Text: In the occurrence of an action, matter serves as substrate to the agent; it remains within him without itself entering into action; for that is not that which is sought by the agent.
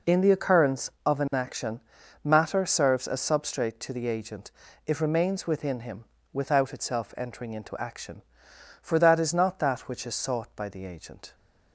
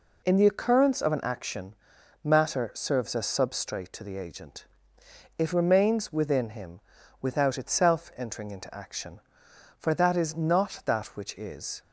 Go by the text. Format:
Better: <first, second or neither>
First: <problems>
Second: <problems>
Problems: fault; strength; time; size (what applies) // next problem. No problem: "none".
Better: first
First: pauses between "him" and "without"; slight; at 6.0 s; 0.28 s long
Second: pauses between "him" and "without"; at 6.7 s; 0.42 s long // stops before "sought by the agent"; at 11.8 s